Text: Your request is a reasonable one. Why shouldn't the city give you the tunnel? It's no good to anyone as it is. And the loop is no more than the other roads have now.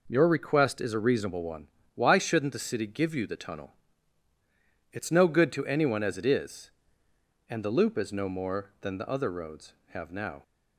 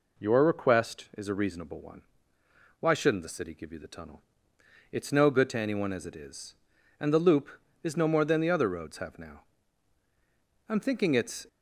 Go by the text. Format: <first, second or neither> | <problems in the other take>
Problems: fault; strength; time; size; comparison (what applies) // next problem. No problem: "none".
first | goes on to say "I'm thinking it's"; noticeable; from 10.6 s on; 0.78 s long